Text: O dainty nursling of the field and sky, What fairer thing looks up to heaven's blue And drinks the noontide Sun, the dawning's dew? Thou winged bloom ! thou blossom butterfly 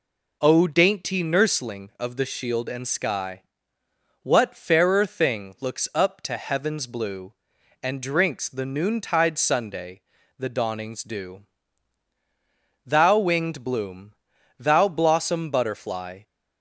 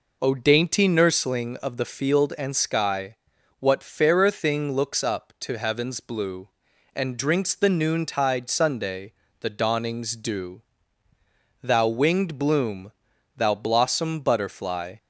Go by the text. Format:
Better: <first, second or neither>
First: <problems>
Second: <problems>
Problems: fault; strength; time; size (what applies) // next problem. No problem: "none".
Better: second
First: says "shield" for "field"; at 2.2 s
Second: none